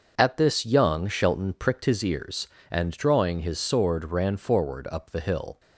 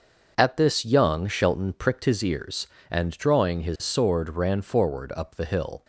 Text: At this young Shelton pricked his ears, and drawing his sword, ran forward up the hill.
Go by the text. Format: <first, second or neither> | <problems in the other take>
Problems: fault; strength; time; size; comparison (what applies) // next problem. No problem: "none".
neither | starts louder than the rest; the same in both